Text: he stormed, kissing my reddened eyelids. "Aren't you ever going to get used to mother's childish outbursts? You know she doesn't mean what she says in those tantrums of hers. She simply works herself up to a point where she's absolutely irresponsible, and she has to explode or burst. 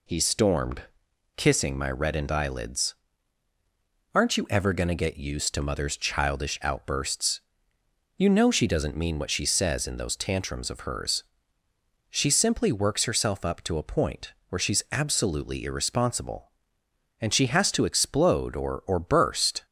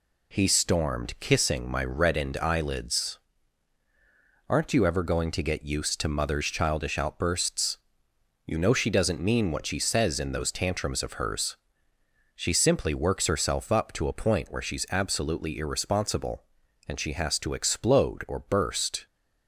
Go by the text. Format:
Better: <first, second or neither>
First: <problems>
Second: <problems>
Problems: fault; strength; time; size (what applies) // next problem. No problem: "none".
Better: second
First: pauses between "point" and "where"; slight; at 14.3 s; 0.16 s long // says "or" twice; at 18.8 s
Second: none